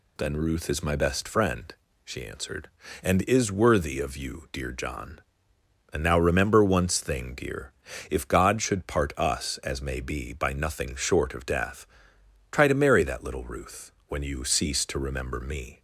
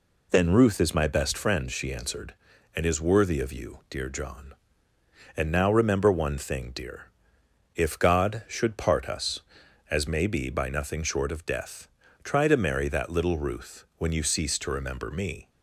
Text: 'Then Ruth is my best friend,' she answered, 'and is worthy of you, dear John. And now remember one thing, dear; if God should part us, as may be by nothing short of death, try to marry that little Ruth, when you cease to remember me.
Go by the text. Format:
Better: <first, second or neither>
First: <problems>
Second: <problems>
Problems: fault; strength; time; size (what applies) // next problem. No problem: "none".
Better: second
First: says "once" for "one"; at 6.6 s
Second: none